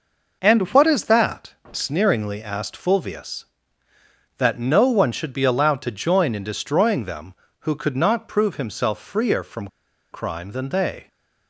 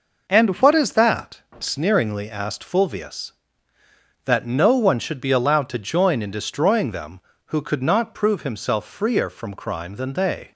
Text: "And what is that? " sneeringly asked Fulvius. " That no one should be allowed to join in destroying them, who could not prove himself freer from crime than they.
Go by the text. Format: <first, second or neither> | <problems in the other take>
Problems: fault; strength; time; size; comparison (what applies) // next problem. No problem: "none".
second | pauses between "from" and "crime"; at 9.6 s; 0.44 s long